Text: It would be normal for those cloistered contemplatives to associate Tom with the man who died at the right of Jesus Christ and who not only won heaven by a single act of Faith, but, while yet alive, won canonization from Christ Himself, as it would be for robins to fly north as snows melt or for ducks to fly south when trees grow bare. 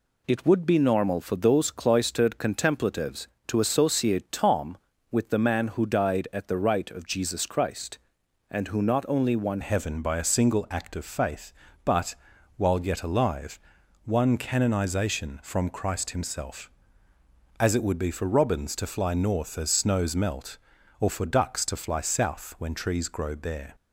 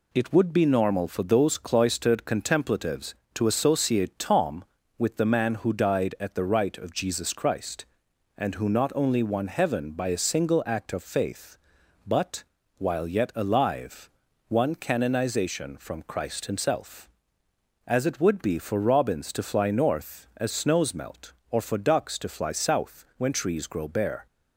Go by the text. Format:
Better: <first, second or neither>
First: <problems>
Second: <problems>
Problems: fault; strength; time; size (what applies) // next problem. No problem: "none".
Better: second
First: changes voice at "heaven"; from 9.6 s on; 14.1 s long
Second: none